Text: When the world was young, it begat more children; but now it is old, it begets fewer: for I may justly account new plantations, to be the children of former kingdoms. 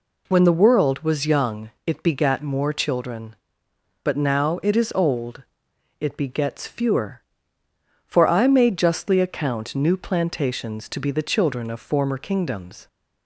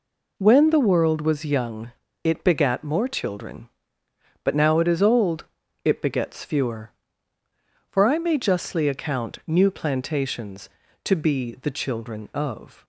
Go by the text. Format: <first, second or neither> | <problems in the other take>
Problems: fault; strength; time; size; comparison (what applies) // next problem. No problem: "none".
first | stops before "former kingdoms"; at 12.8 s